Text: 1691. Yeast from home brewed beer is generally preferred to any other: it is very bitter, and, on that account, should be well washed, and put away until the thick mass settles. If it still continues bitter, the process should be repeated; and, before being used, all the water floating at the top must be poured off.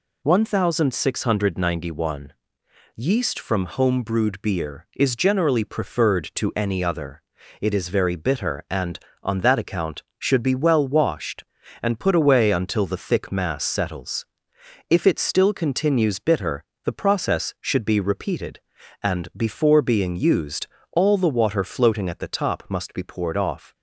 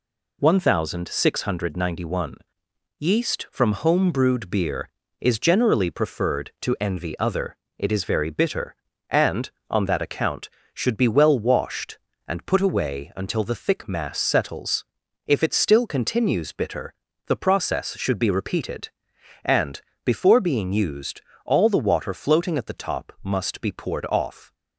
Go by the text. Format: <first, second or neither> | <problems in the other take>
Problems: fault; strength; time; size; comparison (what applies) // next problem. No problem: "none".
first | says "envy" for "any"; at 6.7 s